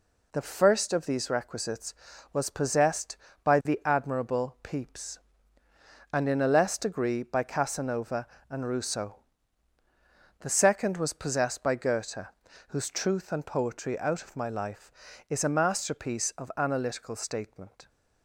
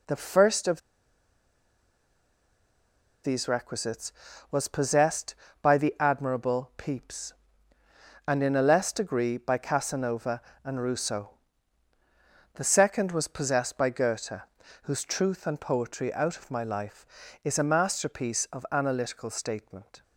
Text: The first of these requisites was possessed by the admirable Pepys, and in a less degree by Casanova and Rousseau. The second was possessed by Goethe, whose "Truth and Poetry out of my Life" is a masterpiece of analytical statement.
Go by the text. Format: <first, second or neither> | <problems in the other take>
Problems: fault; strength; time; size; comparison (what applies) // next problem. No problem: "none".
first | pauses between "of" and "these"; strong; at 0.8 s; 2.4 s long